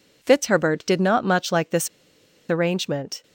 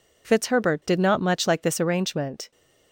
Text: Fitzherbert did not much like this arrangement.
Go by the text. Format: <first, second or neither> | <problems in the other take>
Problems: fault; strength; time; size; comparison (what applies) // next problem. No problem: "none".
second | pauses between "this" and "arrangement"; noticeable; at 1.8 s; 0.62 s long